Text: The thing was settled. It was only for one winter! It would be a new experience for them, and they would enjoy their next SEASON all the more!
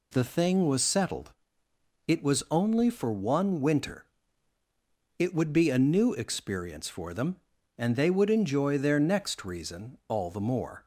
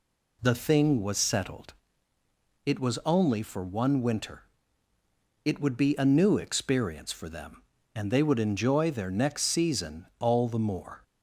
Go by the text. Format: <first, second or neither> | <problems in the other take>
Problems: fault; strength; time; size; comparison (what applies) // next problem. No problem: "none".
second | says "Reason" for "SEASON"; at 9.4 s